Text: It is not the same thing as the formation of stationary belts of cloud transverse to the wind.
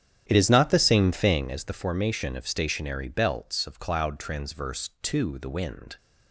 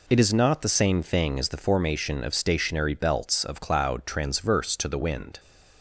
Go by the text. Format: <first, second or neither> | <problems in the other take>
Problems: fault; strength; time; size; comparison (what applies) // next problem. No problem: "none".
second | starts louder than the rest; strong; until 1.5 s; 10 dB